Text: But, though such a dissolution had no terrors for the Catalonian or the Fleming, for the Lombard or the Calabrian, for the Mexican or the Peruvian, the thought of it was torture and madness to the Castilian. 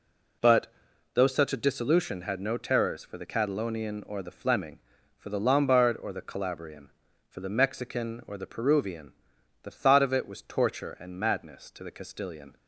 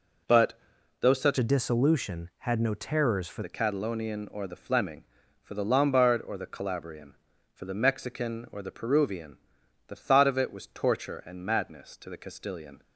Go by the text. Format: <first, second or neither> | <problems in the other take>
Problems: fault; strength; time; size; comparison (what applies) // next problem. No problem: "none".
first | changes voice from "a" to "for"; from 1.3 to 3.4 s; 2.1 s long